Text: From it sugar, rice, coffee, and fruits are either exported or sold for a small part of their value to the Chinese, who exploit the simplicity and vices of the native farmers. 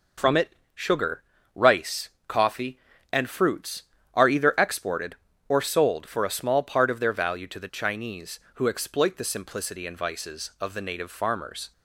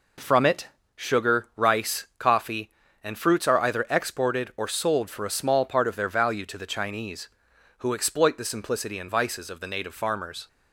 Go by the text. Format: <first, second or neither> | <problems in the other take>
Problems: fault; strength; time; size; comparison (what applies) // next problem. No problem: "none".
neither | pauses between "it" and "sugar"; slight; the same in both